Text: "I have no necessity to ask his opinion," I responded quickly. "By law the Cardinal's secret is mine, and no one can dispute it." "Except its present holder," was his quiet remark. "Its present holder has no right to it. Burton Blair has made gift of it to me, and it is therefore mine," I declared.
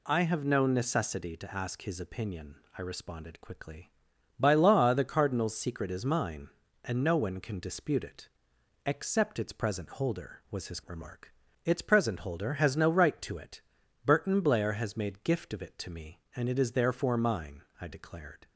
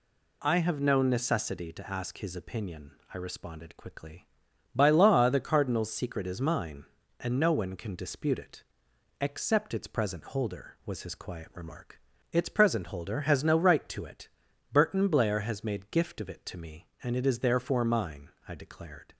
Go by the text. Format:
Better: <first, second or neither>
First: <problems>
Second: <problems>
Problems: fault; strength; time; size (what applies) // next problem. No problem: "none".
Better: second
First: skips "quiet"; at 10.8 s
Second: none